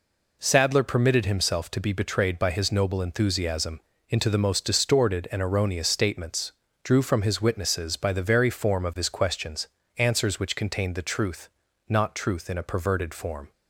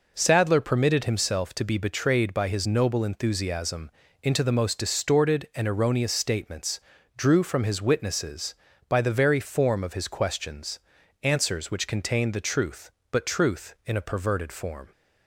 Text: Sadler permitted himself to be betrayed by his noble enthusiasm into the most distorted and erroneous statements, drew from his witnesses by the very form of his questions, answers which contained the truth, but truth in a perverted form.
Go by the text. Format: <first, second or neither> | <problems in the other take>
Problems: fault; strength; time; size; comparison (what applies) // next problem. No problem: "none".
second | pauses between "enthusiasm" and "into"; slight; at 3.8 s; 0.28 s long; slight in the second // says "not" for "but"; at 11.8 s